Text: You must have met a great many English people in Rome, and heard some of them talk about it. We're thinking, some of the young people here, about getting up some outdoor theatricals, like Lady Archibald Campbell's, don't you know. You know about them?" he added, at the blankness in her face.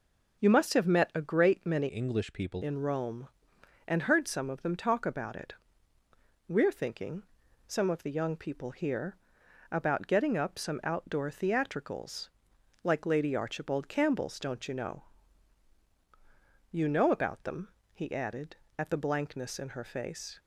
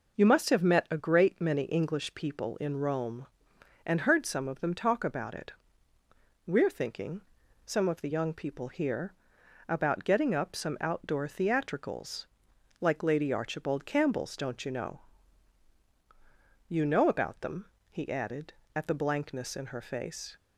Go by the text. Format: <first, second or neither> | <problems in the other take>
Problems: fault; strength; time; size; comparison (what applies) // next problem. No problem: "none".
second | changes voice from "English" to "people"; from 1.8 to 2.6 s; 0.8 s long